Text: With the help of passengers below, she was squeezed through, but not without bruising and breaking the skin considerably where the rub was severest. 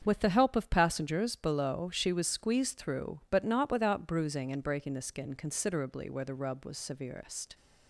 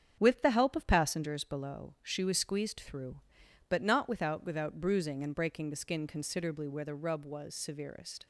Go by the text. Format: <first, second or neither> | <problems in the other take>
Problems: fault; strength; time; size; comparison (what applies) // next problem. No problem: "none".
first | starts louder than the rest; strong; until 1.2 s; 8 dB; strong in the first // says "without" twice; at 4.4 s